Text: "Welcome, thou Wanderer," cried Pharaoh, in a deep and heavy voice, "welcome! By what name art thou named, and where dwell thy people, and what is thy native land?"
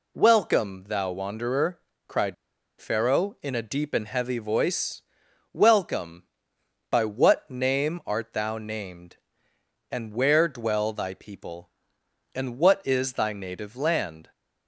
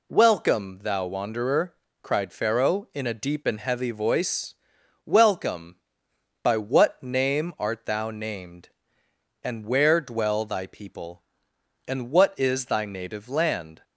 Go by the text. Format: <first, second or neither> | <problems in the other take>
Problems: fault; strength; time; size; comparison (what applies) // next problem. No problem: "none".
second | pauses between "cried" and "Pharaoh"; at 2.3 s; 0.45 s long